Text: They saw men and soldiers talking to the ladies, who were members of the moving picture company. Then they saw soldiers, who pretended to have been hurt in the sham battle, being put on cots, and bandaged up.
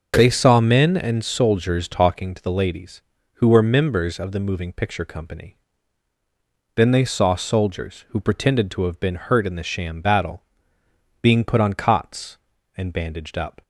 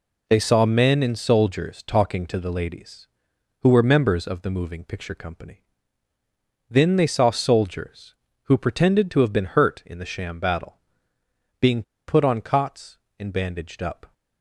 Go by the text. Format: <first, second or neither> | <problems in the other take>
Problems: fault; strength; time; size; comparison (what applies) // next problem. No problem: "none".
first | pauses between "being" and "put"; slight; at 11.8 s; 0.24 s long